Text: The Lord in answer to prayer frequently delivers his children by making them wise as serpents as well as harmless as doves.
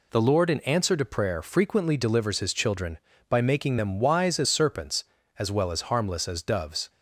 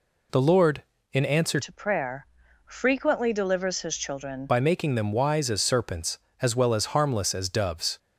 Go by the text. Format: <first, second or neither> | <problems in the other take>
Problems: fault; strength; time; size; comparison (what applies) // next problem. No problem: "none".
first | changes voice from "to" to "children"; from 1.6 to 4.4 s; 2.8 s long // pauses between "prayer" and "frequently"; at 2.2 s; 0.40 s long